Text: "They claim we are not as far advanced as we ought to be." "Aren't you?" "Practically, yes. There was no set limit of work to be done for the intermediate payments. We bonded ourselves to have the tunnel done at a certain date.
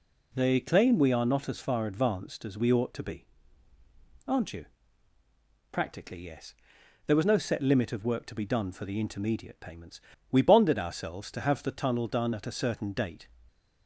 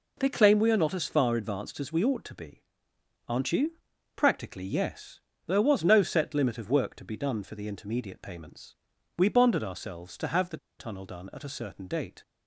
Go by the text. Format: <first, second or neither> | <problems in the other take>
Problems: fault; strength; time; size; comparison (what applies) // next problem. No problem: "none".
first | pauses between "the" and "tunnel"; slight; at 10.5 s; 0.22 s long